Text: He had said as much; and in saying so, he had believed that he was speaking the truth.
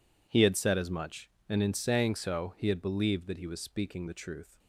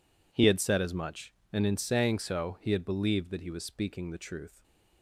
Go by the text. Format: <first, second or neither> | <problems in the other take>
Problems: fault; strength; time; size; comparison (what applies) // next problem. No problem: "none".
neither | none